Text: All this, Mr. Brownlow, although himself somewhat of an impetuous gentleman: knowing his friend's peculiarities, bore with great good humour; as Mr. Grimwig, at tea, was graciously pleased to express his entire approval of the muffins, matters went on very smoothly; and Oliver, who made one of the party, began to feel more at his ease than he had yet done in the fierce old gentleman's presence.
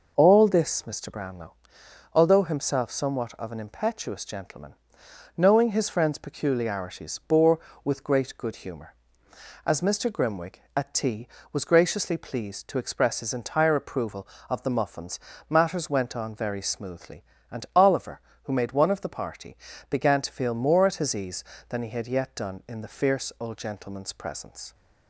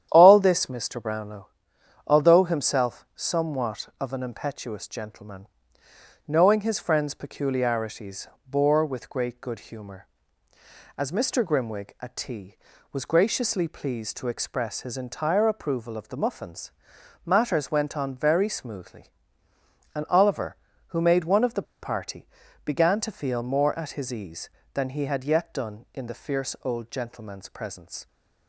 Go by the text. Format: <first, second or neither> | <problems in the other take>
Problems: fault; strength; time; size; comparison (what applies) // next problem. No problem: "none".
first | starts louder than the rest; strong; until 1.1 s; 10 dB // pauses between "the" and "party"; slight; at 21.6 s; 0.19 s long